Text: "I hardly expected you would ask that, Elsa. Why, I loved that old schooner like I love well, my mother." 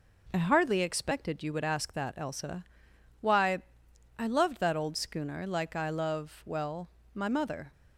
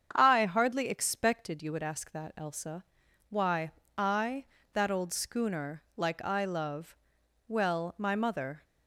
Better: first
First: none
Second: starts louder than the rest; strong; until 1.1 s; 7.5 dB // skips "loved"; at 4.5 s // pauses between "love" and "well"; noticeable; at 6.9 s; 0.50 s long

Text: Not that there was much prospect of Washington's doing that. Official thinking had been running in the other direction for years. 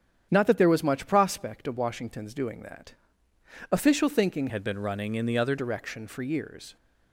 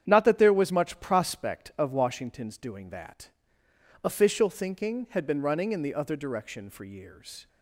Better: second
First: starts louder than the rest; strong; until 1.3 s; 9 dB // changes voice from "had" to "other"; from 4.4 to 5.5 s; 1.1 s long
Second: starts louder than the rest; strong; until 1.0 s; 9 dB

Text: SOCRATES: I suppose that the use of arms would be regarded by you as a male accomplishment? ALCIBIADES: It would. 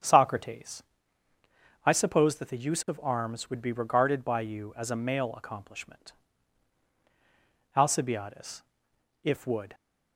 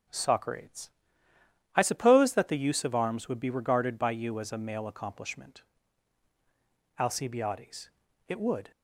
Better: second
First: starts louder than the rest; strong; until 2.0 s; 8 dB // says "If" for "It"; at 9.2 s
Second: none

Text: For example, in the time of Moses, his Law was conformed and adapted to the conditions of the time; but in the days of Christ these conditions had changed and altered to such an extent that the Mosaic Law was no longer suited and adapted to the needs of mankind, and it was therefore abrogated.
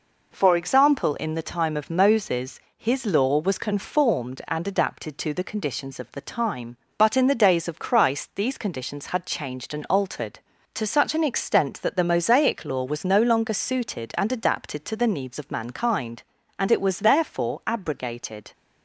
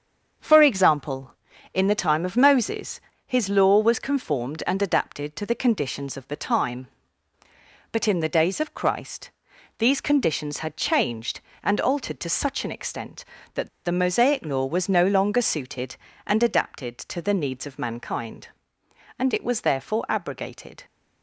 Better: first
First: none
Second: starts louder than the rest; until 1.7 s; 7 dB // pauses between "Christ" and "these"; noticeable; at 9.2 s; 0.48 s long // pauses between "that" and "the"; slight; at 13.6 s; 0.16 s long

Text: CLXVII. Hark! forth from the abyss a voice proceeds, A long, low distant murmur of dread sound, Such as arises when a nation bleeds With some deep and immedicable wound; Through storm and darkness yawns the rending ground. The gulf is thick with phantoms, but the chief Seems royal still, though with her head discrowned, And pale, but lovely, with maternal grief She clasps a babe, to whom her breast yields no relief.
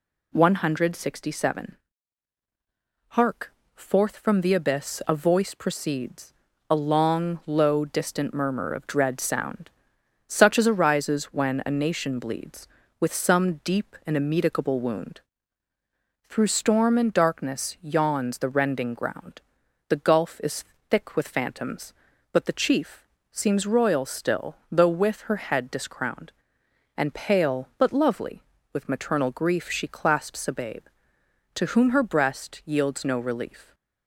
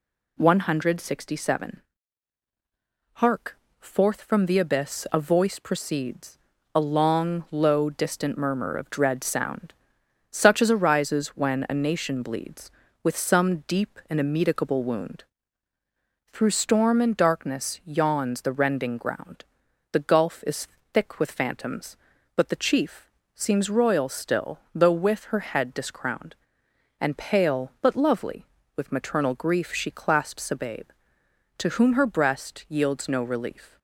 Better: neither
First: pauses between "is" and "thick"; slight; at 20.6 s; 0.24 s long // pauses between "chief" and "Seems"; slight; at 23.0 s; 0.26 s long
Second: pauses between "is" and "thick"; slight; at 20.6 s; 0.24 s long // pauses between "chief" and "Seems"; slight; at 23.0 s; 0.26 s long

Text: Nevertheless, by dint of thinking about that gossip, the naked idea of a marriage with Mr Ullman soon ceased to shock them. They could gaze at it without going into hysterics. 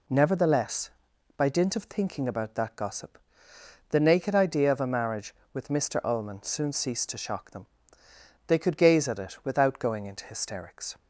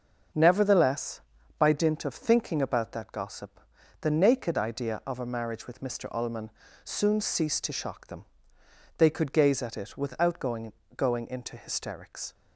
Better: first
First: none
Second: starts louder than the rest; until 1.7 s; 6.5 dB // pauses between "Ullman" and "soon"; slight; at 6.5 s; 0.32 s long // says "going" twice; at 10.9 s

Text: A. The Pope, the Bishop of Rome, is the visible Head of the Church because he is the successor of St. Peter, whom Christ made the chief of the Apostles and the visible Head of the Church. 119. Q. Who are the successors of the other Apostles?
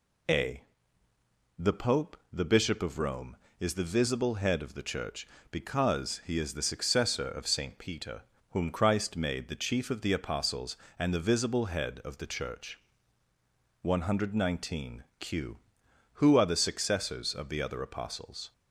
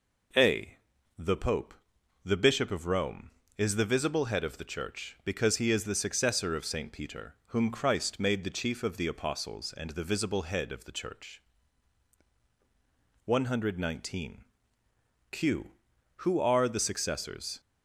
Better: first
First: none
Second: stops before "of the other Apostles"; at 17.5 s

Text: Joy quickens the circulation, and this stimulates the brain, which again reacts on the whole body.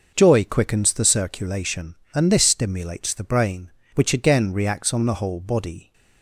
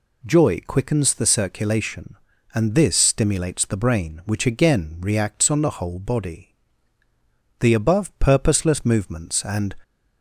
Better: first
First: none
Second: goes on to say "The above purposeless movements and"; strong; from 7.6 s on; 2.1 s long

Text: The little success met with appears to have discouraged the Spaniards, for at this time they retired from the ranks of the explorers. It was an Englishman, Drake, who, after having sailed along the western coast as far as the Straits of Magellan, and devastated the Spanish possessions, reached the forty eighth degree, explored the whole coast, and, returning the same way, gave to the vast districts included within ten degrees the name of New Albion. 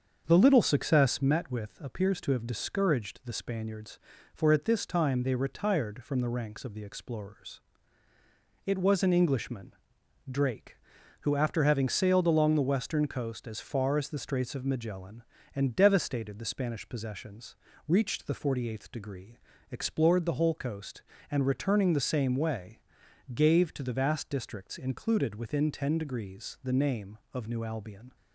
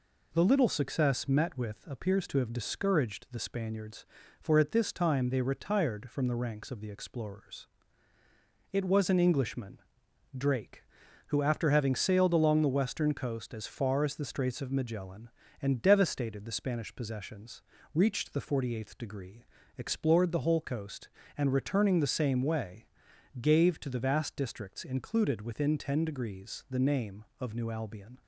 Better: second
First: starts louder than the rest; until 1.2 s; 7 dB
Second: none

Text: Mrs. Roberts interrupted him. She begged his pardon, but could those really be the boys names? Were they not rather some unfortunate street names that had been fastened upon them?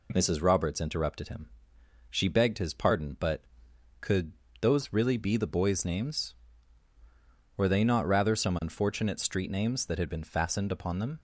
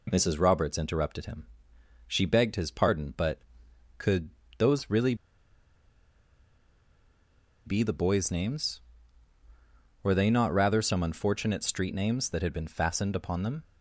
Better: first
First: pauses between "could" and "those"; slight; at 4.3 s; 0.28 s long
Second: pauses between "could" and "those"; slight; at 4.3 s; 0.28 s long // pauses between "really" and "be"; strong; at 5.1 s; 2.5 s long

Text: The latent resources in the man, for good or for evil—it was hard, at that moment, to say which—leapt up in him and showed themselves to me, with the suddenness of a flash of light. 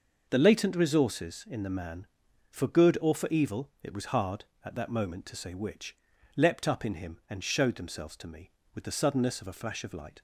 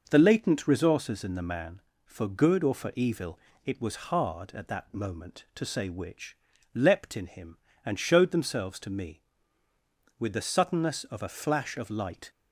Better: first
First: none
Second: skips "up"; at 7.1 s

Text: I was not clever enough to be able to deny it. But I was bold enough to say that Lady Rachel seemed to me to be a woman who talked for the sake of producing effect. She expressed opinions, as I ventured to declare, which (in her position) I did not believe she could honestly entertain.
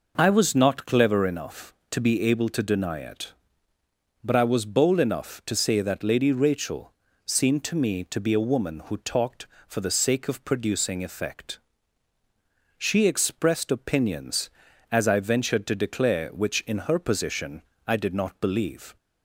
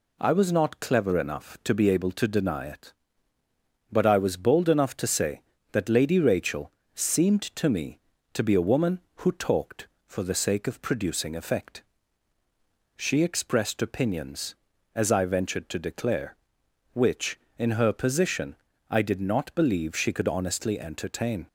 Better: second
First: pauses between "Rachel" and "seemed"; slight; at 6.9 s; 0.32 s long // stops before "she could honestly entertain"; at 18.9 s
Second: pauses between "Rachel" and "seemed"; slight; at 6.7 s; 0.22 s long

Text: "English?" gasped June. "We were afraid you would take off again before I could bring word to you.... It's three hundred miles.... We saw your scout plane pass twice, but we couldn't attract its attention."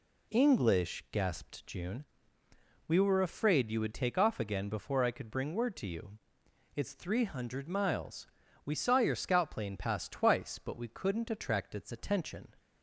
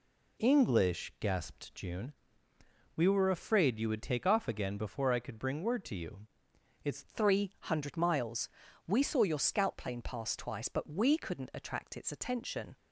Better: first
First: none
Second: changes voice at "three"; from 7.0 s on; 5.7 s long

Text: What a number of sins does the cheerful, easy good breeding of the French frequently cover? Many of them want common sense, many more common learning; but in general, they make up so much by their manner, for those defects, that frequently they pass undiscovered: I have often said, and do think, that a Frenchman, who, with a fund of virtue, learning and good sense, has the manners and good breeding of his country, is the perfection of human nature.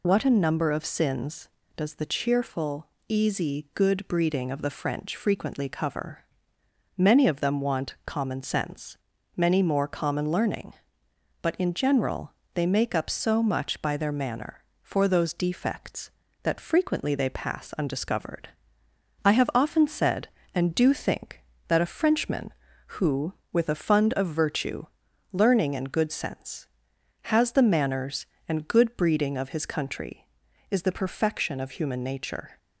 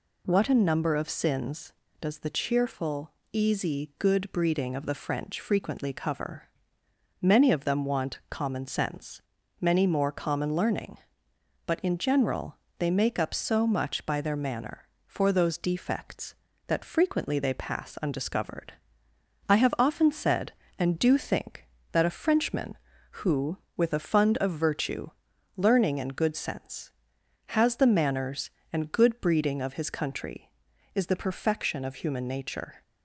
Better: second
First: loses the start of "What"; at 0.0 s; 40 ms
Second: none

